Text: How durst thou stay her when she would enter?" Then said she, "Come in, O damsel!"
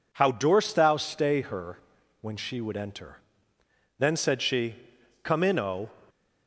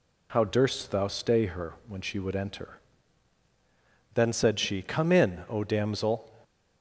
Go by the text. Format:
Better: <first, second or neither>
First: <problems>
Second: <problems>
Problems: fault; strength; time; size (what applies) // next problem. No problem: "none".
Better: second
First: pauses between "her" and "when"; at 1.7 s; 0.42 s long // stops before "damsel"; at 6.0 s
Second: pauses between "her" and "when"; slight; at 1.7 s; 0.16 s long